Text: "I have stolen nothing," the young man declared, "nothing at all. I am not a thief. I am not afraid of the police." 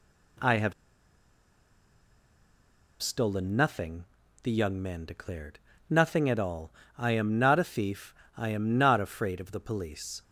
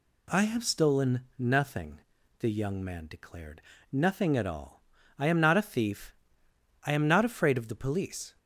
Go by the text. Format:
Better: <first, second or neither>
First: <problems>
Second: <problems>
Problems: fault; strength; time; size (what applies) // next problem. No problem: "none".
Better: second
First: pauses between "have" and "stolen"; strong; at 0.7 s; 2.2 s long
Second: none